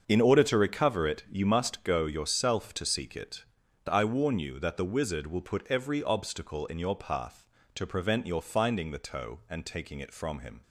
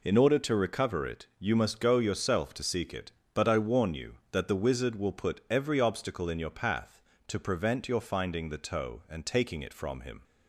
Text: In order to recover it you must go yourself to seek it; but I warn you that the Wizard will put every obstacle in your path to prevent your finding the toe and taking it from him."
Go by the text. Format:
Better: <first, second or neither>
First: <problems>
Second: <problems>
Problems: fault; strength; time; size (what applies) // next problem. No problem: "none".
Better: second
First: starts louder than the rest; until 1.0 s; 6.5 dB // skips "but"; at 3.6 s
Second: none